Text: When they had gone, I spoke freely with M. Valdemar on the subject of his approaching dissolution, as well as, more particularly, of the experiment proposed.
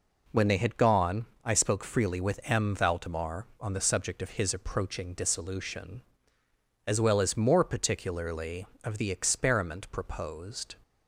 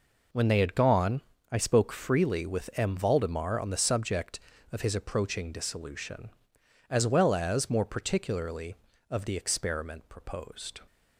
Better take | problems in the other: neither | none

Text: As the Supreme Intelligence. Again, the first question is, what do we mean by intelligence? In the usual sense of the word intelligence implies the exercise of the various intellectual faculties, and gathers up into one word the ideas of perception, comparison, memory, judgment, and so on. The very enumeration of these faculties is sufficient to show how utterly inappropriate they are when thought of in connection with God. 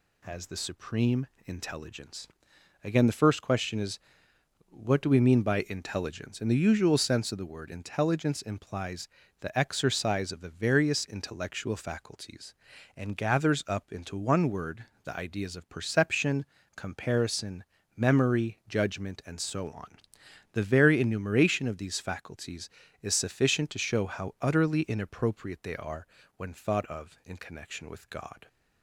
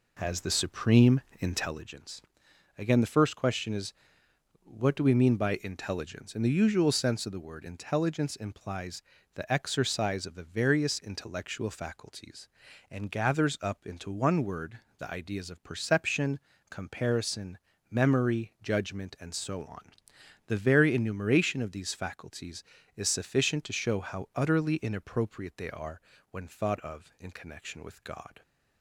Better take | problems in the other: first | starts louder than the rest; slight; until 1.9 s; 3 dB // pauses between "Supreme" and "Intelligence"; slight; at 1.1 s; 0.20 s long; slight in the first // pauses between "implies" and "the"; slight; at 9.0 s; 0.34 s long; slight in the first // pauses between "word" and "the"; slight; at 14.7 s; 0.18 s long; slight in the first // pauses between "are" and "when"; slight; at 25.9 s; 0.32 s long; slight in the first

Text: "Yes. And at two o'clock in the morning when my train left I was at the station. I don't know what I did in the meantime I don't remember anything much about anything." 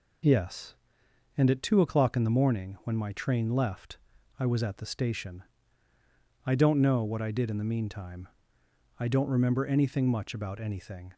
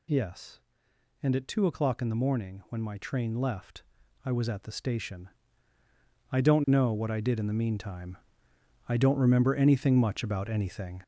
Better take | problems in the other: first | gets louder; strong; throughout; 7 dB // pauses between "left" and "I"; at 3.8 s; 0.42 s long; also in the first // pauses between "meantime" and "I"; noticeable; at 8.1 s; 0.68 s long; noticeable in the first

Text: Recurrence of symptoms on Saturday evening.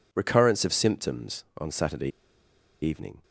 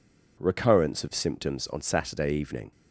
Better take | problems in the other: second | pauses between "Saturday" and "evening"; noticeable; at 2.0 s; 0.73 s long

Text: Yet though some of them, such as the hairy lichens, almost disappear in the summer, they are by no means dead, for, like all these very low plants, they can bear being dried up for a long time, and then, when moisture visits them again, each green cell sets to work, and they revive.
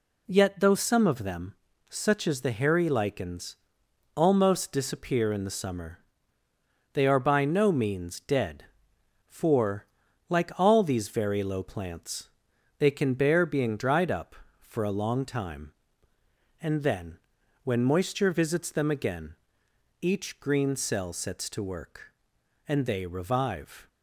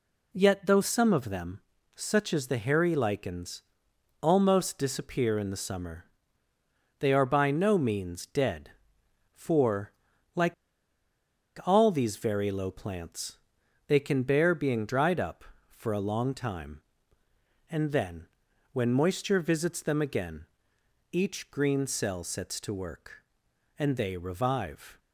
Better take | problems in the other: first | pauses between "like" and "all"; at 10.5 s; 1.1 s long

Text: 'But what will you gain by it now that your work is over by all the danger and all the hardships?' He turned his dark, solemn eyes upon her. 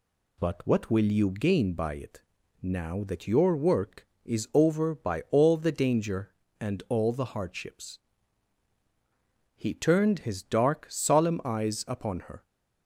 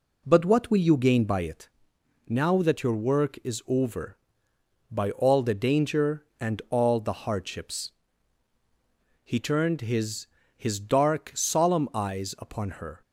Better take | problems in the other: first | pauses between "it" and "now"; noticeable; at 1.6 s; 0.58 s long; also in the first // says "his" twice; at 10.5 s

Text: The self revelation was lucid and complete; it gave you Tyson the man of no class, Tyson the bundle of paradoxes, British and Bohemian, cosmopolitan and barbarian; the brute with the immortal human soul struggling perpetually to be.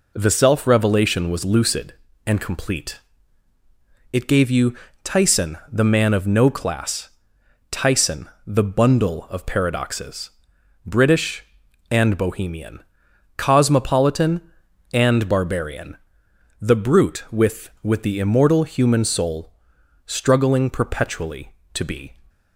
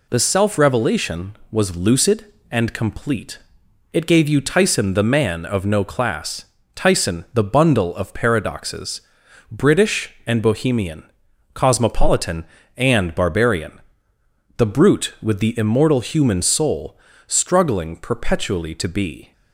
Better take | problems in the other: second | pauses between "you" and "Tyson"; slight; at 4.7 s; 0.28 s long // pauses between "Tyson" and "the"; slight; at 8.2 s; 0.16 s long // says "with" twice; at 17.8 s // pauses between "soul" and "struggling"; noticeable; at 19.5 s; 0.54 s long; slight in the second

